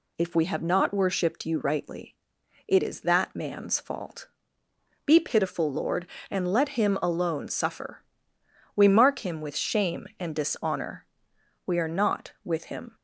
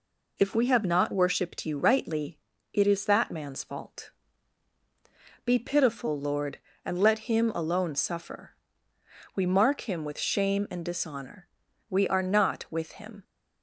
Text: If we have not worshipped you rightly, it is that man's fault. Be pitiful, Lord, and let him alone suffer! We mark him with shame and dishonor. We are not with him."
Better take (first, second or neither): neither